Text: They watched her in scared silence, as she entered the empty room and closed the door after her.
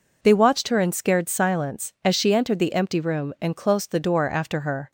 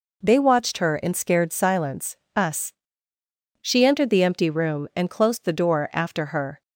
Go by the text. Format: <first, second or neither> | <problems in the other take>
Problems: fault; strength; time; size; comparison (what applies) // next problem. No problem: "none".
first | says "us" for "as"; at 2.3 s